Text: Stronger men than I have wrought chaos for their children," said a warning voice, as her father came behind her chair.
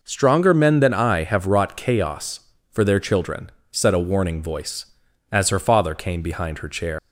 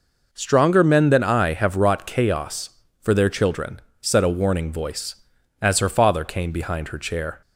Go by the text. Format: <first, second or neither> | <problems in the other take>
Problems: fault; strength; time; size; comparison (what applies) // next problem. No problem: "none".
second | leaves "chair" unfinished; at 6.9 s; 125 ms